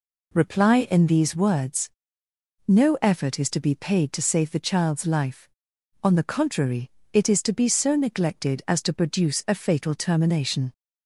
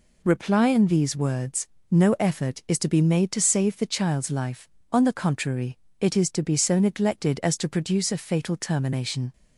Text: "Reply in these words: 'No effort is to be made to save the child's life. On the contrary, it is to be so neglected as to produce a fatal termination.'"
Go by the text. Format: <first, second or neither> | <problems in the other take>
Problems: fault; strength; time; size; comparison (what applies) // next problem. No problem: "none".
second | says "paid" for "made"; at 3.7 s